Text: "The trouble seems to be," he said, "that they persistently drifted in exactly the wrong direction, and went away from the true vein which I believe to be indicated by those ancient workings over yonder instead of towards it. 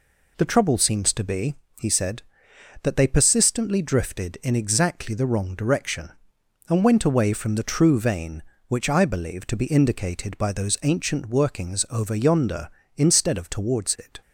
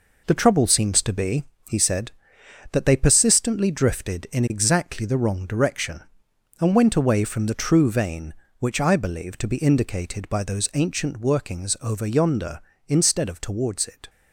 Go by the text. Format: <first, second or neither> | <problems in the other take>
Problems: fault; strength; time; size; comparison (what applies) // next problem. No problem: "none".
first | gets quieter; throughout; 6.5 dB